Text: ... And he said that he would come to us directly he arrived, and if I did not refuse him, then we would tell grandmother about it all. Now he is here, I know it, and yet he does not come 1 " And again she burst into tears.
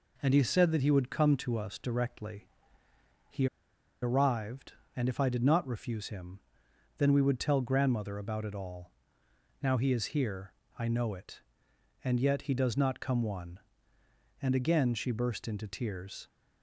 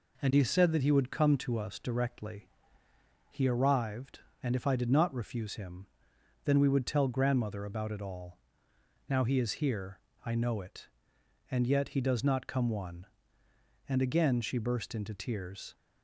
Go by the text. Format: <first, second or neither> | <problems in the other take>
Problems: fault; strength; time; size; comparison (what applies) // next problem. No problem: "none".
second | pauses between "directly" and "he"; noticeable; at 2.4 s; 0.80 s long; noticeable in the second // pauses between "he" and "arrived"; noticeable; at 3.4 s; 0.55 s long